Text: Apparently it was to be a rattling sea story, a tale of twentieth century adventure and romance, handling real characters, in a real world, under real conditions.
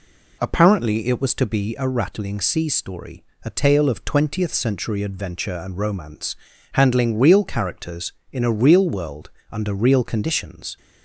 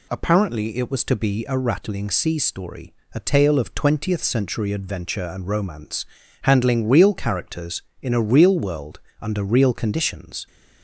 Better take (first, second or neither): second